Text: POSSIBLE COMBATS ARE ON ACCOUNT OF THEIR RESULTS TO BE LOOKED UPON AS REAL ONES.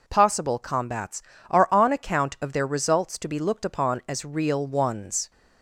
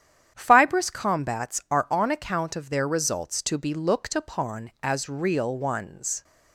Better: first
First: none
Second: starts louder than the rest; strong; until 1.3 s; 9.5 dB // says "Fibrous" for "POSSIBLE"; at 0.3 s

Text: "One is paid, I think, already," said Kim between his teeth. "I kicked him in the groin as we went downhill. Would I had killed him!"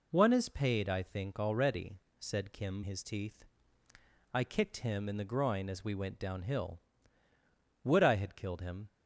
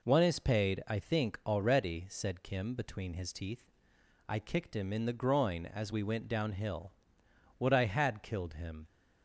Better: second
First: skips "between"; at 2.8 s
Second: none

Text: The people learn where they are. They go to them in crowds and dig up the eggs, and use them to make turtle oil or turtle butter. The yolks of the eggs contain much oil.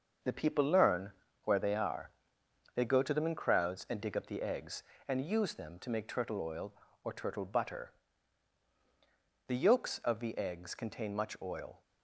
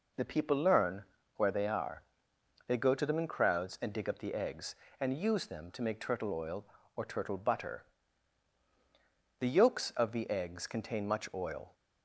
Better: second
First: gets quieter; throughout; 6.5 dB // pauses between "learn" and "where"; slight; at 1.0 s; 0.36 s long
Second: pauses between "learn" and "where"; slight; at 1.0 s; 0.36 s long

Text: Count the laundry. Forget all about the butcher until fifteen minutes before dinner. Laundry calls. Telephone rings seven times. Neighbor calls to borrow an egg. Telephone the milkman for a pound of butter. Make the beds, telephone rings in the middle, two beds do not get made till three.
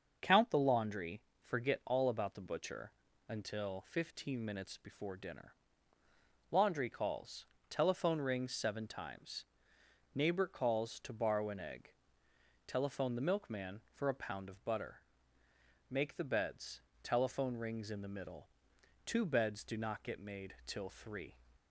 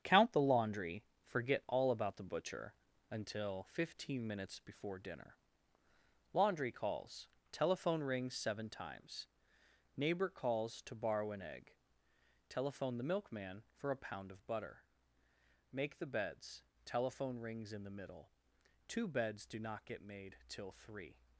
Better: first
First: starts louder than the rest; until 1.4 s; 6.5 dB // pauses between "butcher" and "until"; slight; at 2.9 s; 0.36 s long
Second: gets quieter; strong; throughout; 8 dB // starts louder than the rest; strong; until 1.2 s; 8 dB // pauses between "butcher" and "until"; slight; at 2.7 s; 0.36 s long

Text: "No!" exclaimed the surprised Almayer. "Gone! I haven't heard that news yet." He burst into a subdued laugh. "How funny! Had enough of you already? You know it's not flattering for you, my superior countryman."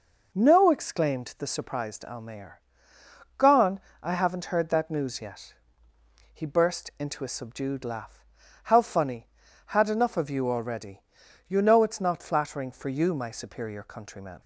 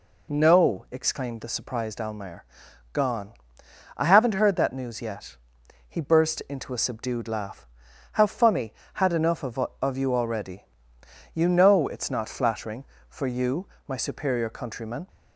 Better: first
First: none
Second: says "of" twice; at 9.8 s

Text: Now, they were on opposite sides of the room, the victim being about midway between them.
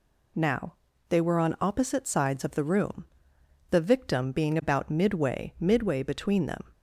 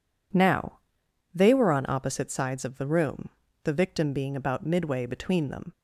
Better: second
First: says "midway" twice; at 5.5 s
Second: none

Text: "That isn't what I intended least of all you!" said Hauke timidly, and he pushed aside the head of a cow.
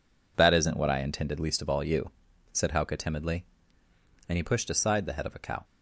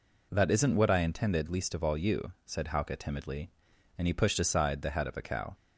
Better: neither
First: none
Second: none

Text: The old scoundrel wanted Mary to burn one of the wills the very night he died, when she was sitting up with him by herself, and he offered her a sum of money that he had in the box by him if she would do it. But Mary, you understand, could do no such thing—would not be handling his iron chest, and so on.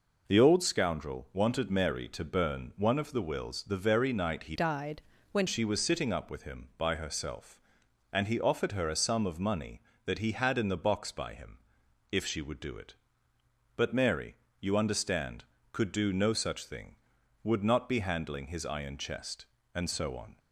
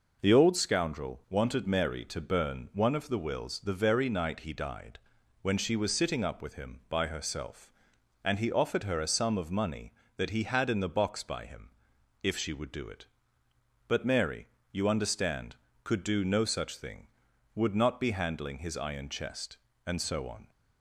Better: second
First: changes voice from "died" to "when"; from 4.5 to 5.4 s; 0.9 s long // pauses between "him" and "if"; noticeable; at 11.5 s; 0.52 s long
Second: pauses between "him" and "if"; noticeable; at 11.6 s; 0.52 s long

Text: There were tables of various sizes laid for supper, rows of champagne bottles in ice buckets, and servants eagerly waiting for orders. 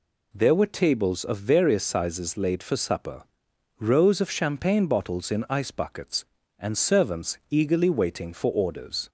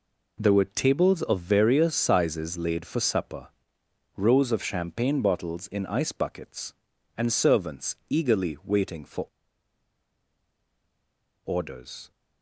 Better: first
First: none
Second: pauses between "for" and "orders"; strong; at 9.2 s; 2.1 s long

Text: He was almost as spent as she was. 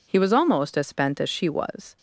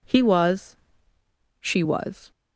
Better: first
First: none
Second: skips "almost as spent as"; at 1.1 s

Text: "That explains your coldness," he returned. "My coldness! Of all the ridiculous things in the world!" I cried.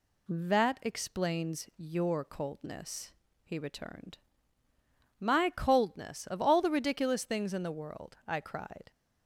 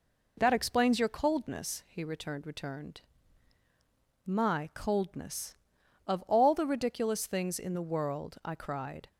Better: first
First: none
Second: says "returned" twice; at 2.4 s

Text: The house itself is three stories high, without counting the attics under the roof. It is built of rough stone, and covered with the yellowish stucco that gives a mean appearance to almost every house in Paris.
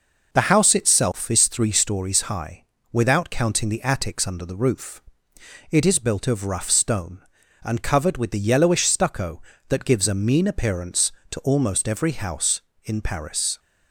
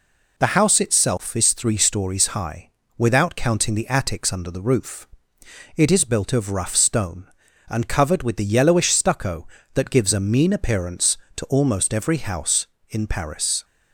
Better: second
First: starts louder than the rest; noticeable; until 1.7 s; 5.5 dB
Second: none

